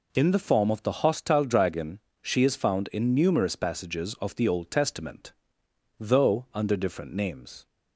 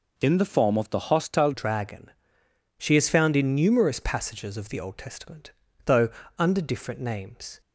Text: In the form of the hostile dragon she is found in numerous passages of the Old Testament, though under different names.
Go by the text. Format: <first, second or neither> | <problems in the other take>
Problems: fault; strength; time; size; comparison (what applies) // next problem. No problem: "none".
first | changes voice at "dragon"; from 1.5 s on; 6.1 s long // pauses between "dragon" and "she"; noticeable; at 2.1 s; 0.68 s long; slight in the first // pauses between "though" and "under"; slight; at 6.0 s; 0.30 s long